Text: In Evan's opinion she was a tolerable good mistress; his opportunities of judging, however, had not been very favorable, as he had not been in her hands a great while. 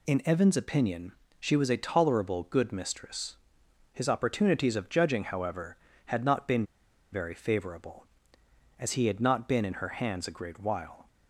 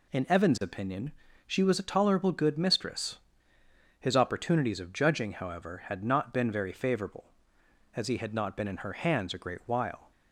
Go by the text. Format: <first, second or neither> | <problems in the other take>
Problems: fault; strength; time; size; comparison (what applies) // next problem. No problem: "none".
second | pauses between "opinion" and "she"; slight; at 1.1 s; 0.26 s long; slight in the second // pauses between "been" and "very"; noticeable; at 6.6 s; 0.49 s long